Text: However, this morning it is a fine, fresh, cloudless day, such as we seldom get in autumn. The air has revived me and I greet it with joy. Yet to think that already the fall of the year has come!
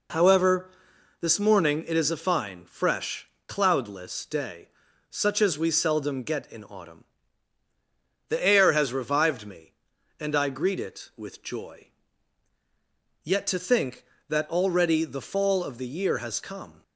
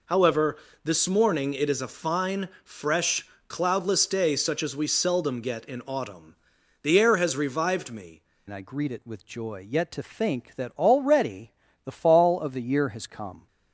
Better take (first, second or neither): first